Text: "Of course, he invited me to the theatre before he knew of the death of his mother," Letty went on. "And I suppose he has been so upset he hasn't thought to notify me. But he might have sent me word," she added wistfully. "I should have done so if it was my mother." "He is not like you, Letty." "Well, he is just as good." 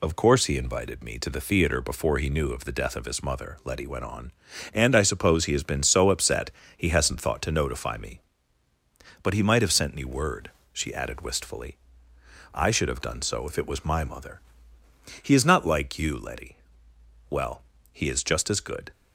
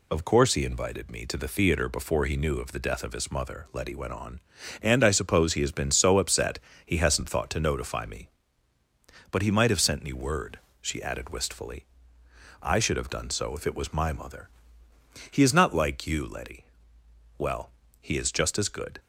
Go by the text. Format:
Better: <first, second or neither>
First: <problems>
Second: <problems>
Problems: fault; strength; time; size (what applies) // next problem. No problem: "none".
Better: neither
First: pauses between "upset" and "he"; slight; at 6.5 s; 0.24 s long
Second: pauses between "upset" and "he"; slight; at 6.5 s; 0.24 s long